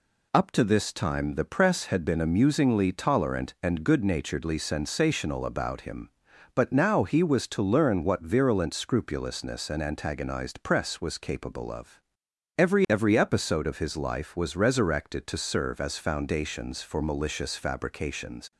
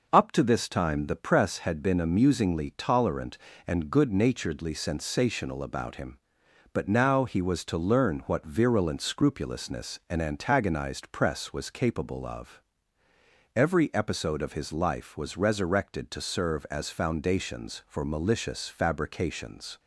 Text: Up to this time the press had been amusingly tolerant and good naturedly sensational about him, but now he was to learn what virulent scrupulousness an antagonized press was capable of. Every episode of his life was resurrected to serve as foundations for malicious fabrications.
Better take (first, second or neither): second